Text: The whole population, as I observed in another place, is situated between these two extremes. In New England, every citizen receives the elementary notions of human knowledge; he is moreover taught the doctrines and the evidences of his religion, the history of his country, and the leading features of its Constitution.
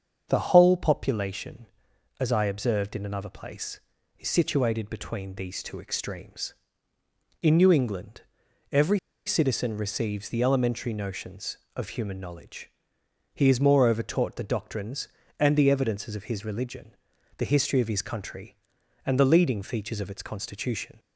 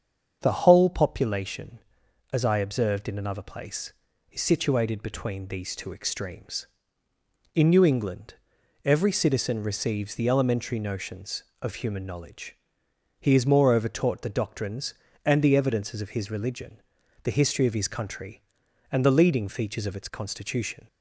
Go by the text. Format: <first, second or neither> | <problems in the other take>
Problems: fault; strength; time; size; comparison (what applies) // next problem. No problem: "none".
second | starts louder than the rest; until 1.2 s; 7 dB; also in the second // pauses between "every" and "citizen"; slight; at 8.9 s; 0.28 s long